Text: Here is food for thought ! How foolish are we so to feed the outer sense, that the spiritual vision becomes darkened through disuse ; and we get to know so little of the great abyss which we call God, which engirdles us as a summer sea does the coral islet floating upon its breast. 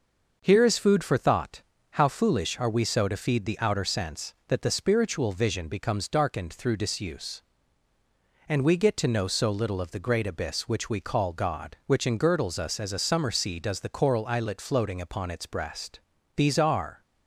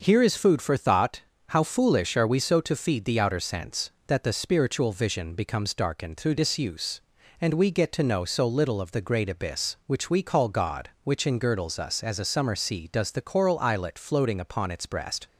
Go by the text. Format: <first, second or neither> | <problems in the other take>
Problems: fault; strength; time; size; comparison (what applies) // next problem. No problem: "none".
second | starts louder than the rest; noticeable; until 1.4 s; 6 dB; noticeable in the second // goes on to say "These are"; noticeable; from 16.3 s on; 0.66 s long